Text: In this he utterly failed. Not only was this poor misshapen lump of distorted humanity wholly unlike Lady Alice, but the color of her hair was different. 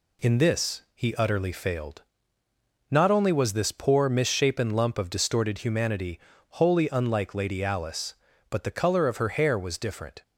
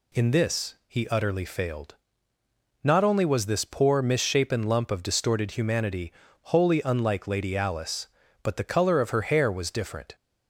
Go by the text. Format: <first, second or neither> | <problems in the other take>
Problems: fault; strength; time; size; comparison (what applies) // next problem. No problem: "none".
second | gets quieter; slight; throughout; 3 dB // pauses between "humanity" and "wholly"; slight; at 6.1 s; 0.36 s long; slight in the second